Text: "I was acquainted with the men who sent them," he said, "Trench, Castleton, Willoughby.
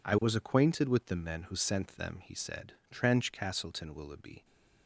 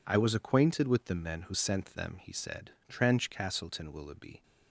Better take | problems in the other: neither | none

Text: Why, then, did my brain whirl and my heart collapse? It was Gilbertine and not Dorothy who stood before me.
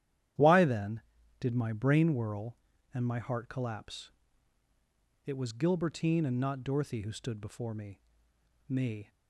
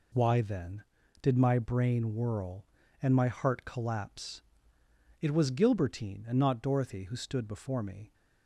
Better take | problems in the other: second | starts louder than the rest; strong; until 1.7 s; 11.5 dB // says "me" twice; at 8.6 s

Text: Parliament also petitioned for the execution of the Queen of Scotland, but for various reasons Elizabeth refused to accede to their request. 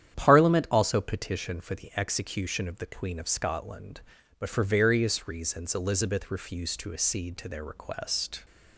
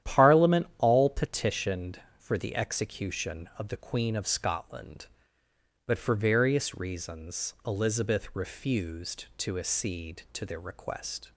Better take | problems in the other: first | starts louder than the rest; strong; until 1.1 s; 11 dB; strong in the first // says "all" for "also"; at 0.7 s

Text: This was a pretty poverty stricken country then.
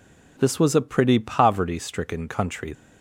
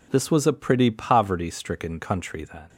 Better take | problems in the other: second | stops before "then"; at 2.7 s

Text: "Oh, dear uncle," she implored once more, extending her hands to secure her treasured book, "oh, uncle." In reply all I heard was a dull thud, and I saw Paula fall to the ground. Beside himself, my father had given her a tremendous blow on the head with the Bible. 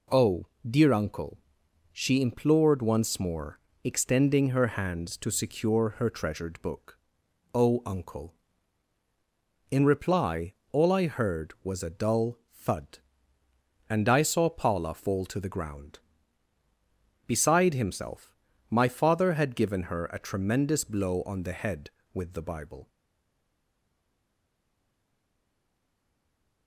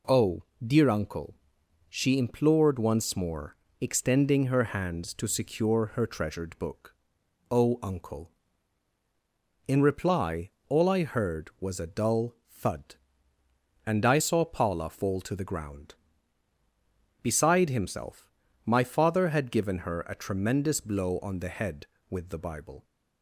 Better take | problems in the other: second | pauses between "reply" and "all"; slight; at 10.5 s; 0.16 s long; slight in the second // stays silent after the last word; strong; from 22.8 s on; 3.8 s long

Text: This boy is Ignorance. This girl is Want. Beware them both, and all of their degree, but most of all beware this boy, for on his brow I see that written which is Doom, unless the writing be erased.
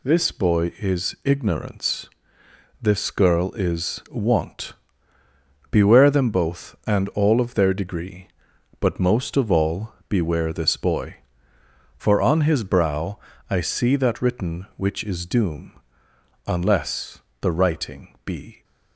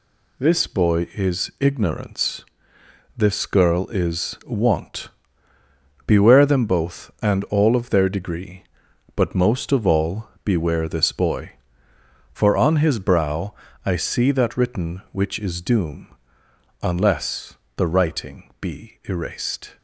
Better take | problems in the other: second | pauses between "all" and "beware"; slight; at 9.9 s; 0.16 s long; slight in the second // pauses between "brow" and "I"; slight; at 13.2 s; 0.28 s long; slight in the second // pauses between "unless" and "the"; slight; at 17.2 s; 0.20 s long; slight in the second // stops before "erased"; at 18.6 s

